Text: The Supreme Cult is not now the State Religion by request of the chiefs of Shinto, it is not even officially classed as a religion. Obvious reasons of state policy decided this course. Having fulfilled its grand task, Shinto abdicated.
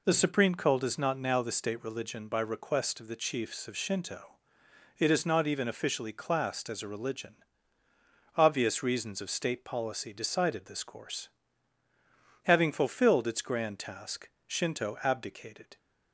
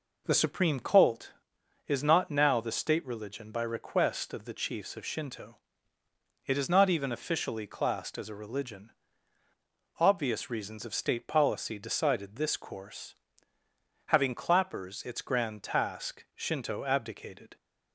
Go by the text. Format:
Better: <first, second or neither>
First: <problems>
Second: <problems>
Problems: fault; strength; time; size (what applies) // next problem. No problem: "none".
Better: first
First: none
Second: says "clappers" for "fulfilled"; at 14.3 s